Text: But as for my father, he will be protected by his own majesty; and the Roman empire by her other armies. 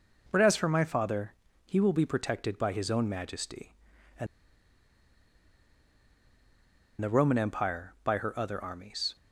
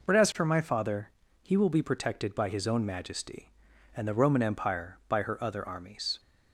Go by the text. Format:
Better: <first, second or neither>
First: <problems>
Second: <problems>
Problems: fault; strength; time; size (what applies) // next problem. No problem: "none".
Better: second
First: pauses between "and" and "the"; strong; at 4.2 s; 2.7 s long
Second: none